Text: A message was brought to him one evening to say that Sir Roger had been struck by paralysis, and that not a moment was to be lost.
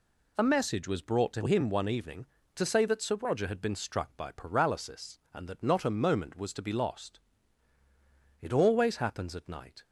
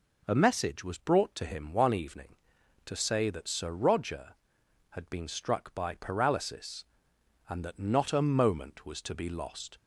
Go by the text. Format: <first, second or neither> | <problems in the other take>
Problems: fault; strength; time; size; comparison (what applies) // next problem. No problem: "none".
second | goes on to say "It always happens at night"; from 8.3 s on; 1.4 s long